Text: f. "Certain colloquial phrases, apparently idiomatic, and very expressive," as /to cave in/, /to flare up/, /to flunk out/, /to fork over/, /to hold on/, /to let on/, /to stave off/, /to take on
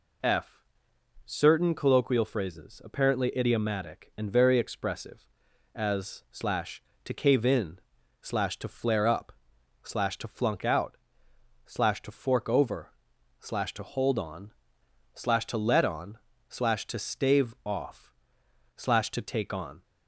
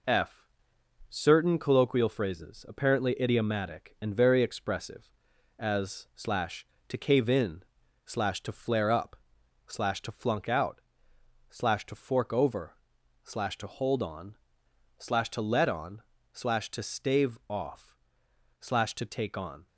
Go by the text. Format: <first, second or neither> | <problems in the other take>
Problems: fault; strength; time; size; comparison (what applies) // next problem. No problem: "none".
first | gets quieter; throughout; 4 dB